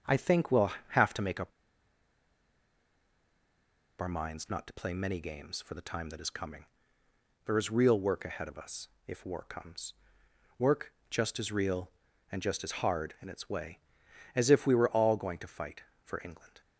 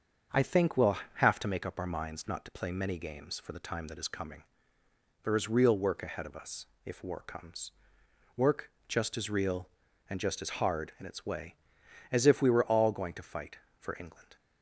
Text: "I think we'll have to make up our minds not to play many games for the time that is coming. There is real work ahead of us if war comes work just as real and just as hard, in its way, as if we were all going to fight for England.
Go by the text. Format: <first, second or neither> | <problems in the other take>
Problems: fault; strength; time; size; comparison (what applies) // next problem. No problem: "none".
second | starts louder than the rest; until 1.2 s; 6.5 dB; also in the second // pauses between "up" and "our"; strong; at 1.5 s; 2.4 s long // pauses between "us" and "if"; slight; at 8.8 s; 0.18 s long; slight in the second // pauses between "comes" and "work"; noticeable; at 9.9 s; 0.64 s long; noticeable in the second // pauses between "work" and "just"; slight; at 10.9 s; 0.18 s long; slight in the second